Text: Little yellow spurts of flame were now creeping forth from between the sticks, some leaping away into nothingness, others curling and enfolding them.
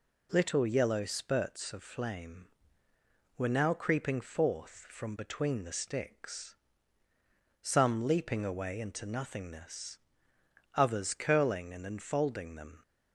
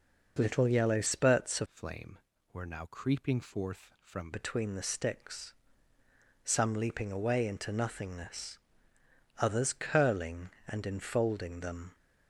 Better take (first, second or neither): first